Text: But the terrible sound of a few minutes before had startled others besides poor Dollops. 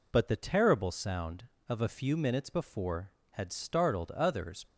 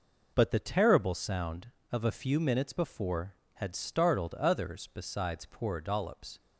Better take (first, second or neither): second